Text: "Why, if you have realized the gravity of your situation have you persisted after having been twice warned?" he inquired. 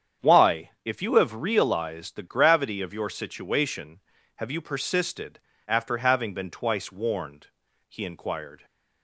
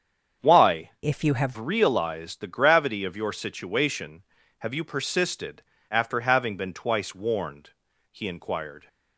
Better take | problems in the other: first | starts louder than the rest; strong; until 1.5 s; 7.5 dB; strong in the first // changes voice from "if" to "have"; from 1.0 to 1.5 s; 0.5 s long // pauses between "persisted" and "after"; slight; at 5.6 s; 0.28 s long; slight in the first

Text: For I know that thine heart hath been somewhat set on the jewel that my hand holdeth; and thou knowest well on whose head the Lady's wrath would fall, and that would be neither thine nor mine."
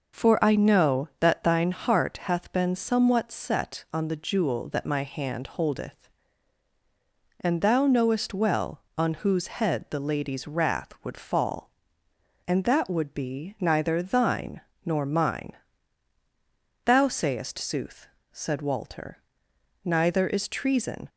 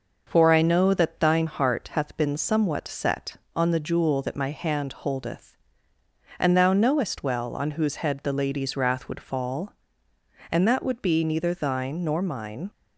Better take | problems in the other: second | pauses between "thine" and "nor"; slight; at 14.6 s; 0.24 s long // goes on to say "Thou sayest sooth said Walter neither is treason"; strong; from 16.8 s on; 4.2 s long

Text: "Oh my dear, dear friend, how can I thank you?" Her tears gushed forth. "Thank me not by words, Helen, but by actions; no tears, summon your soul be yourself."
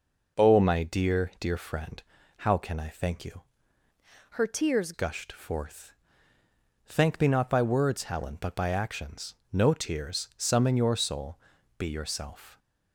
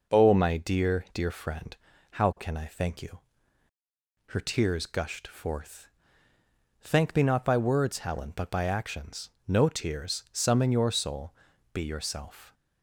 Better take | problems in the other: second | changes voice from "Her" to "tears"; from 4.3 to 4.9 s; 0.6 s long // pauses between "soul" and "be"; at 11.3 s; 0.38 s long; also in the second

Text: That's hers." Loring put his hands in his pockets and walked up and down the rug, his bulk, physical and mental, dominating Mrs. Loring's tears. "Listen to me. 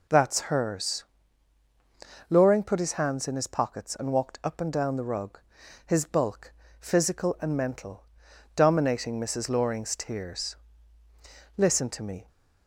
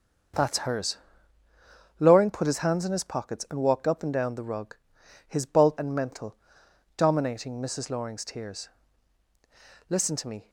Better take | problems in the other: first | starts louder than the rest; until 2.3 s; 6 dB // skips "physical"; at 5.7 s

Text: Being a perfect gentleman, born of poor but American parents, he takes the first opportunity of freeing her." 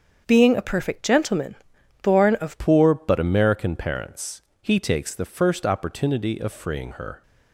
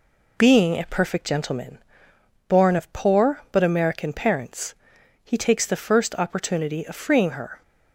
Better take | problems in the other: second | starts louder than the rest; strong; until 1.2 s; 7 dB // changes voice at "poor"; from 2.5 s on; 4.7 s long

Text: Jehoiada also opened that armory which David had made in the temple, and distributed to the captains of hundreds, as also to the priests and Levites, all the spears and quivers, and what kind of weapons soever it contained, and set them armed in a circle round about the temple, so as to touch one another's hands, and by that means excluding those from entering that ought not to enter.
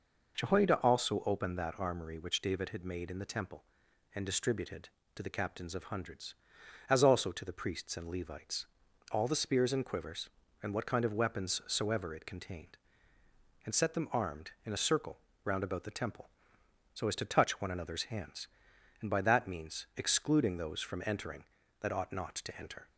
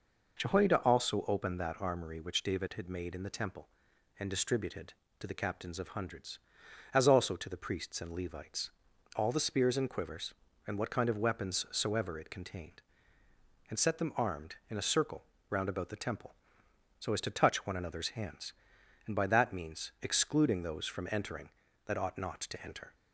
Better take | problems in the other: neither | pauses between "circle" and "round"; slight; the same in both

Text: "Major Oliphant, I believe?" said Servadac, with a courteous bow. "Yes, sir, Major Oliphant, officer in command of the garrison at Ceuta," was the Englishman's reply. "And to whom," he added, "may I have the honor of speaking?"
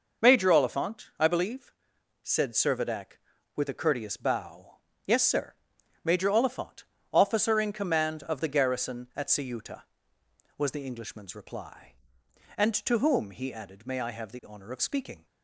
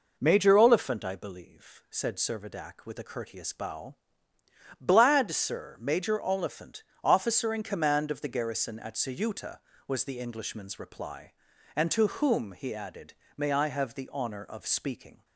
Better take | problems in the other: first | says "Blad" for "Yes"; at 4.7 s

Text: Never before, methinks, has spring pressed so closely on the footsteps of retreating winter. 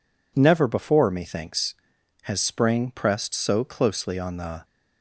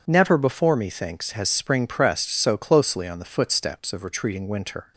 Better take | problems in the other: second | stops before "footsteps of retreating winter"; at 4.6 s

